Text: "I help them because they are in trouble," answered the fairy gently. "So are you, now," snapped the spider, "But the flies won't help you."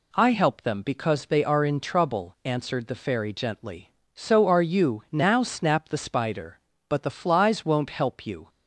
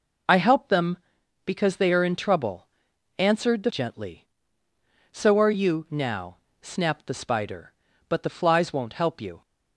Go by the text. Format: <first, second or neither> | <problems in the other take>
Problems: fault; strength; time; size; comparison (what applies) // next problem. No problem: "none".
first | skips "fairy"; at 3.7 s